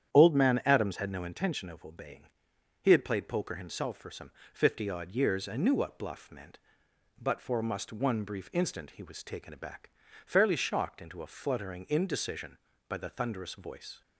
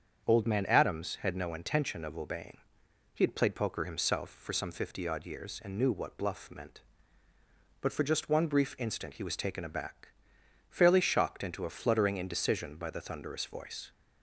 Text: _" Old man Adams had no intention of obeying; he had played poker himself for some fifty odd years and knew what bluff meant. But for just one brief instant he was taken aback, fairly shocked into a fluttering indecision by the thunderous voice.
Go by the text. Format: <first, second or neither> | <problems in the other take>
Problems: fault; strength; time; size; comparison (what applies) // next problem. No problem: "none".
second | starts louder than the rest; strong; until 1.1 s; 9.5 dB; also in the second // pauses between "some" and "fifty"; slight; at 4.2 s; 0.22 s long // says "must" for "just"; at 7.6 s